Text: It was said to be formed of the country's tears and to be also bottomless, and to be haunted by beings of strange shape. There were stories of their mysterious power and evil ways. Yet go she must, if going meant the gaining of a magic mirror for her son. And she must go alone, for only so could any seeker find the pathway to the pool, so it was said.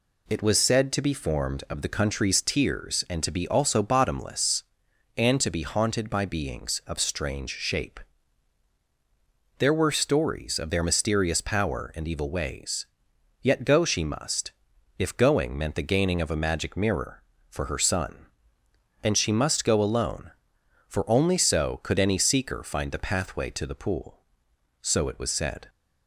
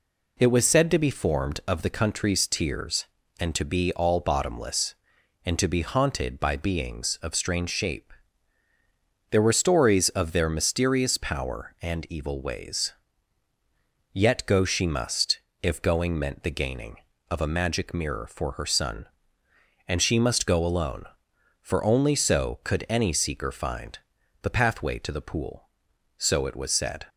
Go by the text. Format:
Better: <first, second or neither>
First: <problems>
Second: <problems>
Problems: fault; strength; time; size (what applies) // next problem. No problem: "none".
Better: first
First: none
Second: says "all" for "also"; at 3.9 s // pauses between "find" and "the"; noticeable; at 23.9 s; 0.46 s long